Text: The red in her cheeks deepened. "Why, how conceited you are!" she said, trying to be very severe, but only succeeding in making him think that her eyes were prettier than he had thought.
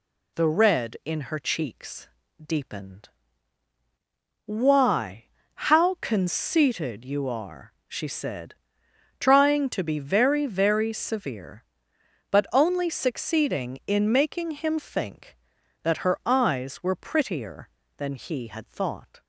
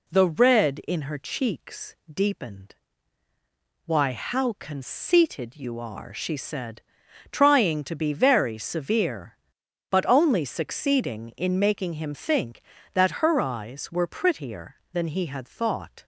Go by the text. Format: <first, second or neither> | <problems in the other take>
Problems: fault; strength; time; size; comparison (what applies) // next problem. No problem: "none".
second | pauses between "cheeks" and "deepened"; slight; at 2.0 s; 0.34 s long // says "very" twice; at 10.4 s